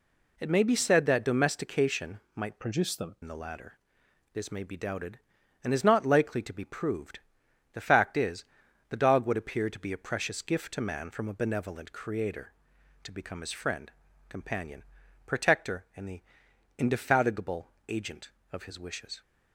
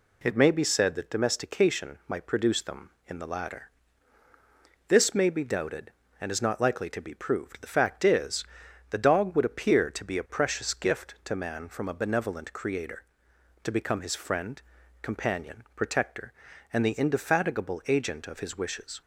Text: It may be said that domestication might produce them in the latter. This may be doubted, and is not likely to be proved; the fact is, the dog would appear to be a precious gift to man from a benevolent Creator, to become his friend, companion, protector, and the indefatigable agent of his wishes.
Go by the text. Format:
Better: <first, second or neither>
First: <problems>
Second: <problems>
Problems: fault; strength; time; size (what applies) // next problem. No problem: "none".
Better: second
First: changes voice from "produce" to "them"; from 2.5 to 3.1 s; 0.6 s long // pauses between "the" and "indefatigable"; noticeable; at 16.2 s; 0.58 s long // pauses between "indefatigable" and "agent"; slight; at 17.6 s; 0.18 s long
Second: none